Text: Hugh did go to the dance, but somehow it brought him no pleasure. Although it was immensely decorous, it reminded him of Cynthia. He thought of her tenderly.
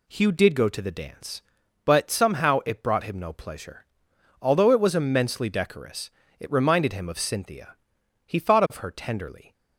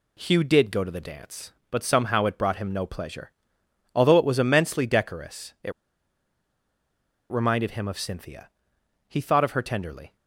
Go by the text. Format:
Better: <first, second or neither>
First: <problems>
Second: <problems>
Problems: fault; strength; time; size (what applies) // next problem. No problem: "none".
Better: first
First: none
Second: pauses between "it" and "reminded"; strong; at 5.7 s; 1.6 s long